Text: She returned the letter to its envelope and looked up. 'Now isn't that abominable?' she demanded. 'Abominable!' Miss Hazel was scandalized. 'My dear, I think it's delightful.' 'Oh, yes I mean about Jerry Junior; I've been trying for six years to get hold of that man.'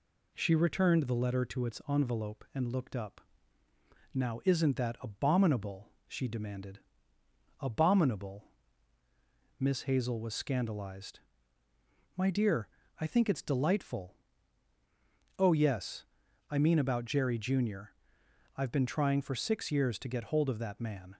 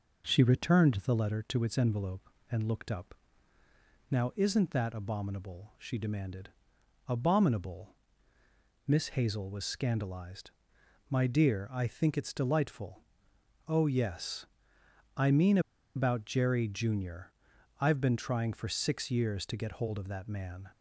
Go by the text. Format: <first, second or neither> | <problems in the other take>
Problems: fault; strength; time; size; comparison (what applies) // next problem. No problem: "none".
first | pauses between "yes" and "I"; noticeable; at 14.4 s; 0.68 s long; also in the first // pauses between "mean" and "about"; at 15.5 s; 0.36 s long